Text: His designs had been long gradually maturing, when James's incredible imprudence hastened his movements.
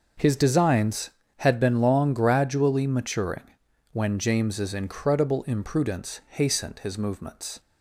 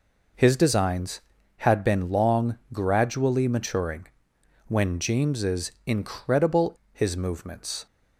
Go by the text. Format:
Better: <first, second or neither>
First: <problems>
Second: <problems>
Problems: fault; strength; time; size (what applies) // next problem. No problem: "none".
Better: first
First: none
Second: pauses between "long" and "gradually"; slight; at 2.5 s; 0.16 s long // skips "imprudence hastened"; at 6.8 s